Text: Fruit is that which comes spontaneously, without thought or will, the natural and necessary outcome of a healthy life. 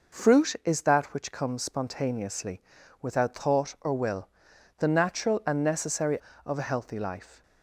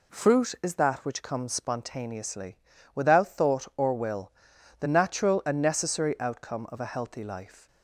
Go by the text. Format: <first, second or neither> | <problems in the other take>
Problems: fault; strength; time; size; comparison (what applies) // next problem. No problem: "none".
second | skips "outcome"; at 6.3 s